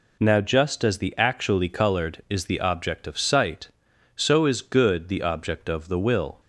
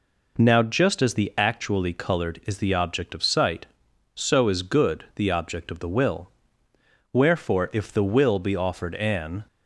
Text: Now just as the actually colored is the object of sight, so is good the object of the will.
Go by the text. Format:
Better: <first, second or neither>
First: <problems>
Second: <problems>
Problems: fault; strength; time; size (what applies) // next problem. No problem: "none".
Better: first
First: none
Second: goes on to say "Wherefore if the will be offered an"; strong; from 7.1 s on; 2.3 s long